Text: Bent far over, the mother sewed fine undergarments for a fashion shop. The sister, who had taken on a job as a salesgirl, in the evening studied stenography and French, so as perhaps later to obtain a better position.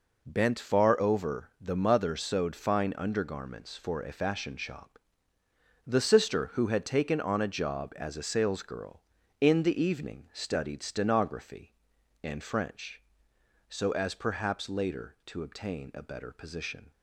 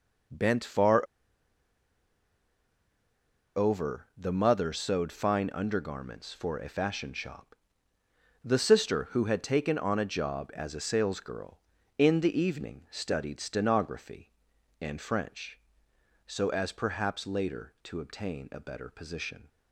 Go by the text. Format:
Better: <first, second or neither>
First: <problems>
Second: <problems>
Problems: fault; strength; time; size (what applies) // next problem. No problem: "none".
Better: first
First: none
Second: pauses between "far" and "over"; strong; at 1.0 s; 2.5 s long